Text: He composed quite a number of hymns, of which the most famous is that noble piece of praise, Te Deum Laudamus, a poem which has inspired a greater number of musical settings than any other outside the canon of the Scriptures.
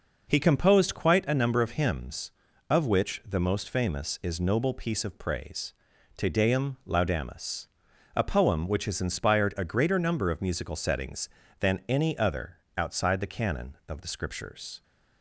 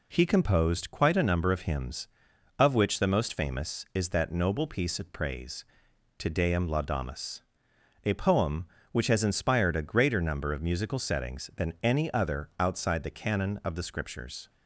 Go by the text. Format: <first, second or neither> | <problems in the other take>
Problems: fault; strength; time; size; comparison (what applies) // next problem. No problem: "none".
second | skips "that"; at 4.3 s // pauses between "other" and "outside"; slight; at 12.5 s; 0.20 s long